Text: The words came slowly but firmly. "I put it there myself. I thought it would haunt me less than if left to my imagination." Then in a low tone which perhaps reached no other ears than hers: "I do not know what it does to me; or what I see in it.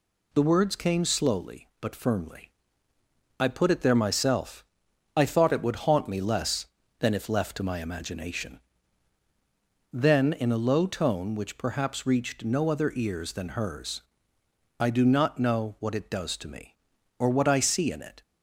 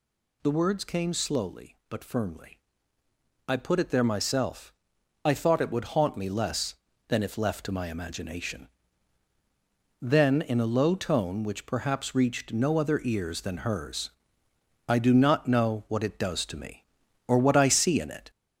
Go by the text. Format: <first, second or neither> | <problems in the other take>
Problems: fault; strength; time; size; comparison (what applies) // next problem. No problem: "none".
first | gets louder; throughout; 4 dB